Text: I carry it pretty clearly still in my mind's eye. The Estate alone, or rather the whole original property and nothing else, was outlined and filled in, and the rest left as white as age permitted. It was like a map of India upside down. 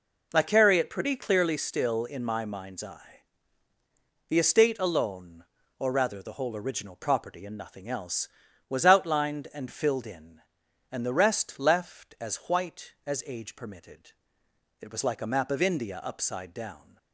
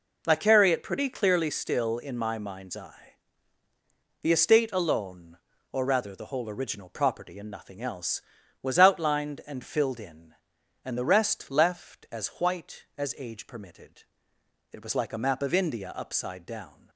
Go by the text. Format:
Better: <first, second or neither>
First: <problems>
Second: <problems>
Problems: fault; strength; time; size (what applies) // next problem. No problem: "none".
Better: neither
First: none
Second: none